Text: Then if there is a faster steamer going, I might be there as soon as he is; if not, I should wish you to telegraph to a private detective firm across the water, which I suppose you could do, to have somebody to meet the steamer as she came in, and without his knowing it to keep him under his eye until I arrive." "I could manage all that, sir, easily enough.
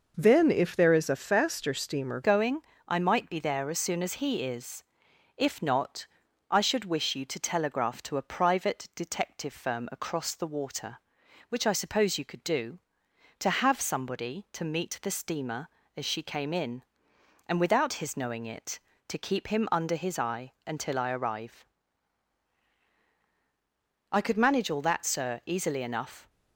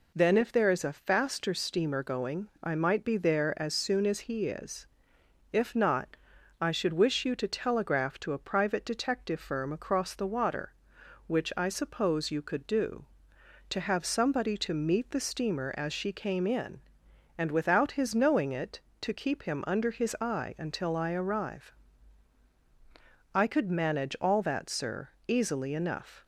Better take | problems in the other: second | changes voice at "going"; from 2.2 s on; 24.0 s long

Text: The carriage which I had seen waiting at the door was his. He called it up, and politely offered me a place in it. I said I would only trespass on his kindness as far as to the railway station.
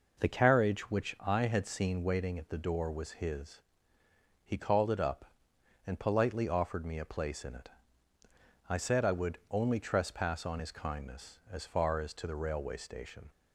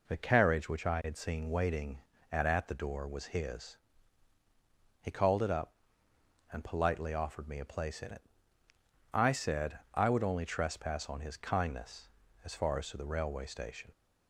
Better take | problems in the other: first | says "at" twice; at 2.4 s

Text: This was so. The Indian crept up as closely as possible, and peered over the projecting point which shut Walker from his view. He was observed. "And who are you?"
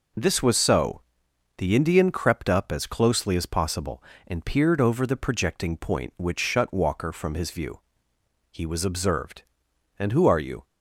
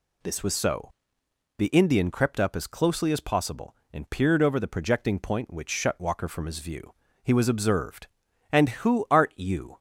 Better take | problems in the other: first | says "art" for "are"; at 9.1 s

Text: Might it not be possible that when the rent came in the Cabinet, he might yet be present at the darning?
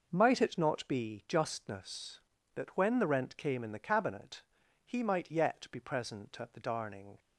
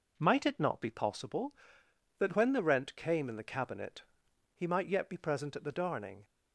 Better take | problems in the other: second | says "justness" for "possible"; at 1.2 s

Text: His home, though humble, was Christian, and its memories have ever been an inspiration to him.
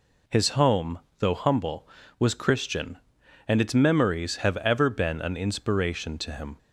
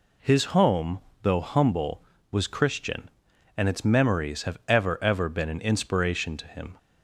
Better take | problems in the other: first | says "ever" twice; at 5.0 s

